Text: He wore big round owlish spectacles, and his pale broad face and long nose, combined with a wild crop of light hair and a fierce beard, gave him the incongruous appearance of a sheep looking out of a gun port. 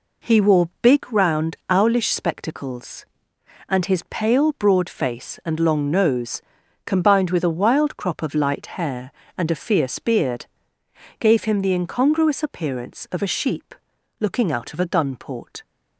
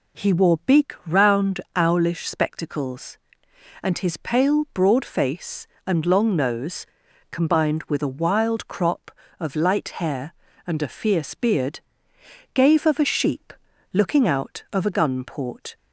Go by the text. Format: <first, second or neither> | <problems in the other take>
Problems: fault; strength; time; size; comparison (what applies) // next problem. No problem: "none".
first | pauses between "round" and "owlish"; slight; at 1.5 s; 0.16 s long // skips "him the incongruous appearance"; at 12.8 s // pauses between "sheep" and "looking"; at 13.5 s; 0.40 s long; noticeable in the first